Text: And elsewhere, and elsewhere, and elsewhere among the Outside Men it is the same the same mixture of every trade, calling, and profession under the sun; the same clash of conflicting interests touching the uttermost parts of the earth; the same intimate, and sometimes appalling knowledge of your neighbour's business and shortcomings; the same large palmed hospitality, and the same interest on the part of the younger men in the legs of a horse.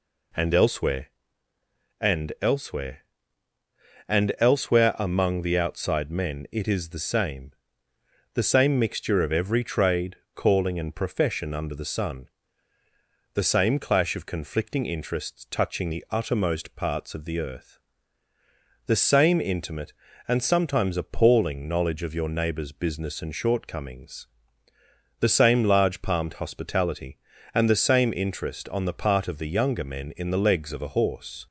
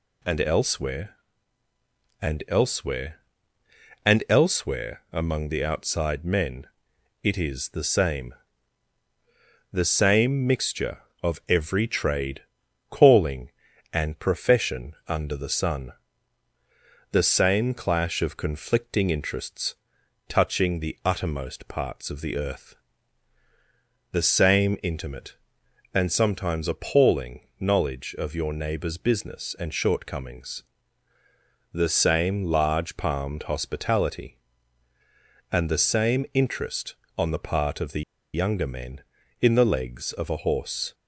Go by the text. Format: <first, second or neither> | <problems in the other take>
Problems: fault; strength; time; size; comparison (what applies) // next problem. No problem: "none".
first | pauses between "Men" and "it"; noticeable; at 6.6 s; 0.58 s long // pauses between "same" and "the"; strong; at 8.3 s; 1.3 s long; noticeable in the first // pauses between "profession" and "under"; slight; at 14.9 s; 0.16 s long // pauses between "interests" and "touching"; noticeable; at 19.7 s; 0.52 s long // pauses between "appalling" and "knowledge"; slight; at 27.3 s; 0.20 s long // pauses between "the" and "younger"; slight; at 38.0 s; 0.32 s long